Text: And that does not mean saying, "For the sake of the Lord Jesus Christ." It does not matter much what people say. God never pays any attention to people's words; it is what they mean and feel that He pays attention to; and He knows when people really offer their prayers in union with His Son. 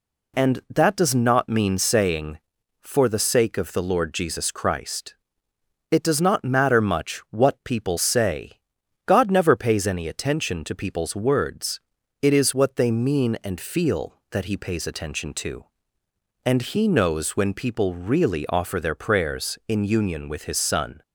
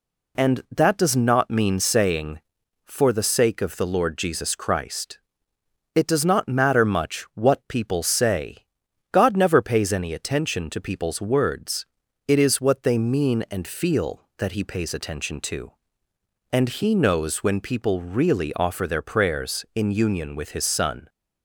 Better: neither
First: none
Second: none

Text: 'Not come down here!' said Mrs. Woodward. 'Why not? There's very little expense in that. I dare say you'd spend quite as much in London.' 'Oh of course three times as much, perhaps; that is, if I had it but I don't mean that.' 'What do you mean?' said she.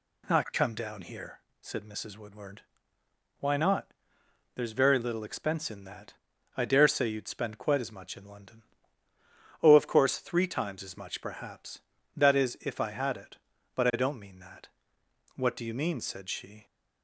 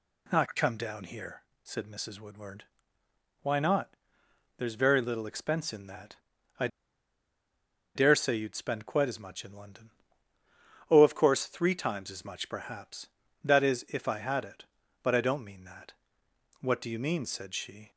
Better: first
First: none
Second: pauses between "I" and "dare"; strong; at 6.6 s; 1.2 s long

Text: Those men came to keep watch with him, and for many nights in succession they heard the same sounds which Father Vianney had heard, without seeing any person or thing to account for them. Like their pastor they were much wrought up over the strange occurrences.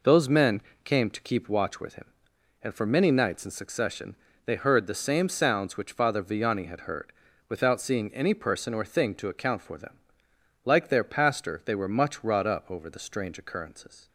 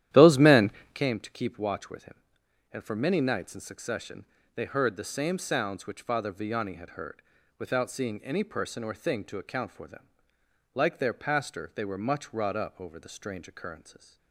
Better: first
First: pauses between "men" and "came"; slight; at 0.6 s; 0.22 s long // pauses between "succession" and "they"; slight; at 4.1 s; 0.30 s long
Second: starts louder than the rest; strong; until 1.0 s; 12 dB // pauses between "men" and "came"; slight; at 0.7 s; 0.22 s long // pauses between "succession" and "they"; slight; at 4.2 s; 0.30 s long

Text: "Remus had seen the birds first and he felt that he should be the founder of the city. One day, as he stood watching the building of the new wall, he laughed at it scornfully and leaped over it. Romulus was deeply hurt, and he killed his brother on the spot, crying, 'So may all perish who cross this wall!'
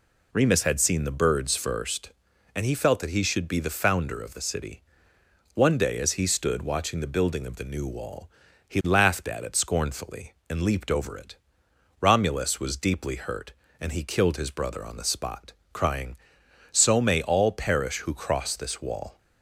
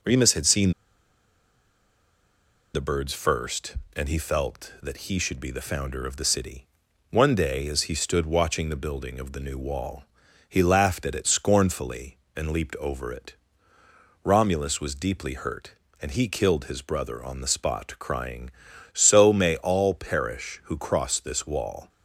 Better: first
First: none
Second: pauses between "seen" and "the"; strong; at 0.7 s; 2.0 s long

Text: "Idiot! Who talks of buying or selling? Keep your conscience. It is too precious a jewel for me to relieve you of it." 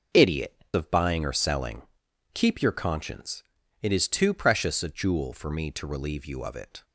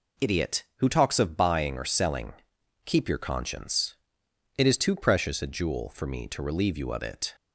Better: second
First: skips "Who talks"; at 0.6 s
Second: none

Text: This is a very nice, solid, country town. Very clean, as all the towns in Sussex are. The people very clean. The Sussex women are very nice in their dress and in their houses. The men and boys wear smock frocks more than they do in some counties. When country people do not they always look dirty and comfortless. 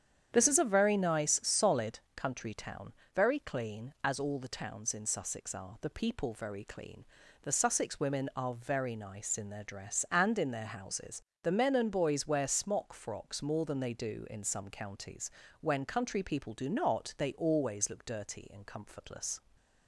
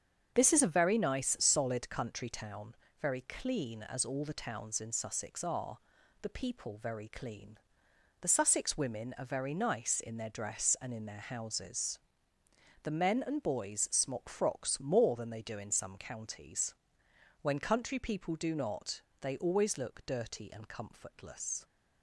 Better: first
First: starts louder than the rest; strong; until 1.3 s; 9 dB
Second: starts louder than the rest; strong; until 1.3 s; 7.5 dB // skips "wear"; at 13.8 s // pauses between "not" and "they"; slight; at 19.0 s; 0.20 s long

